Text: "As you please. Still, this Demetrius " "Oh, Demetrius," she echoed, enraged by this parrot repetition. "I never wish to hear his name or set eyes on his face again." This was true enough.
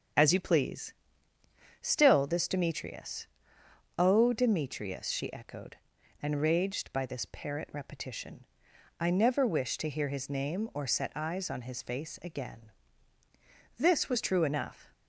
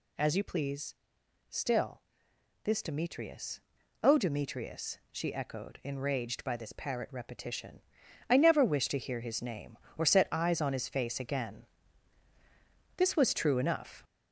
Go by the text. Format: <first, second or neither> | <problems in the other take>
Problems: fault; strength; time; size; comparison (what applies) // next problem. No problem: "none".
first | gets louder; throughout; 7 dB